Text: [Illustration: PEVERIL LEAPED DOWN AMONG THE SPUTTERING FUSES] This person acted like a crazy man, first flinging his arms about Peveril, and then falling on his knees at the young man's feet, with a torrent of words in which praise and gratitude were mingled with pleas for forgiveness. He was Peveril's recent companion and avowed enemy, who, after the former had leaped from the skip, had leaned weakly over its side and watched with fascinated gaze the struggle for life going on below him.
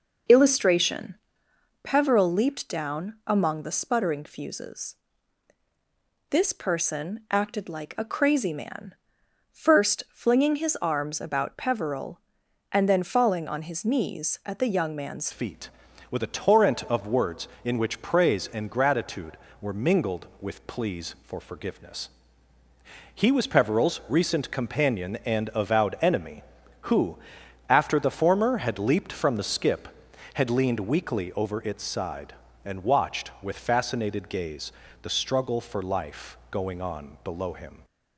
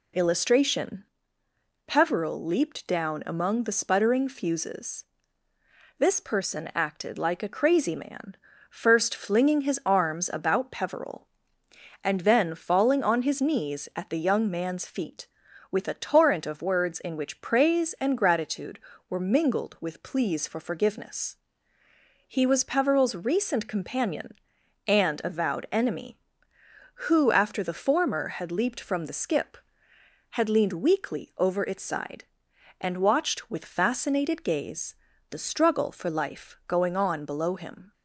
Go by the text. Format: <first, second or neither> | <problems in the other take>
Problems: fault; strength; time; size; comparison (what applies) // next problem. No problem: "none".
second | pauses between "FUSES" and "This"; strong; at 4.9 s; 1.3 s long; noticeable in the second // changes voice at "feet"; from 15.3 s on; 22.5 s long // pauses between "gaze" and "the"; slight; at 34.7 s; 0.30 s long; slight in the second